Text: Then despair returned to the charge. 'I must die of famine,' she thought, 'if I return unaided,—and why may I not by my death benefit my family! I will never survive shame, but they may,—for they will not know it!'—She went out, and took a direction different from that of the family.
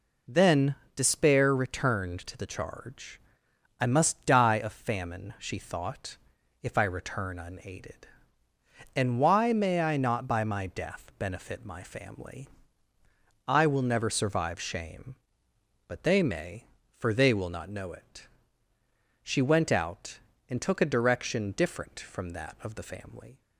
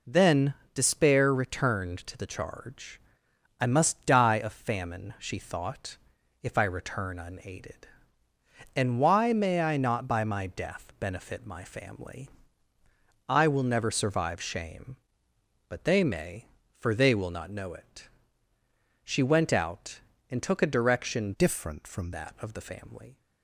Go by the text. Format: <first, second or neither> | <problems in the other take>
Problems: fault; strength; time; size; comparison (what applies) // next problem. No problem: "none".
first | pauses between "Then" and "despair"; slight; at 0.5 s; 0.20 s long; slight in the first // changes voice from "different" to "from"; from 21.3 to 22.1 s; 0.8 s long